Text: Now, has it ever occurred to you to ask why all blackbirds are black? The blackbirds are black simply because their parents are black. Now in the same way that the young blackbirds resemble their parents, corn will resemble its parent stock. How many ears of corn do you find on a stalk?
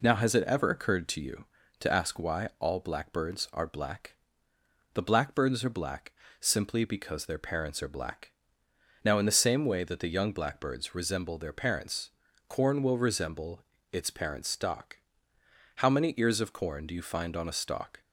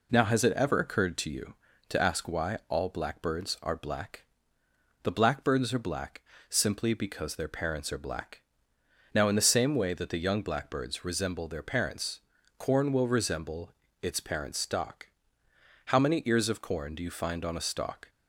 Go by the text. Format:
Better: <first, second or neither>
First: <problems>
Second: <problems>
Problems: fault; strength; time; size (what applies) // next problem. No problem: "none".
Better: neither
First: pauses between "black" and "simply"; slight; at 6.1 s; 0.28 s long // pauses between "resemble" and "its"; slight; at 13.6 s; 0.32 s long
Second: pauses between "black" and "simply"; slight; at 6.2 s; 0.28 s long // pauses between "resemble" and "its"; slight; at 13.7 s; 0.32 s long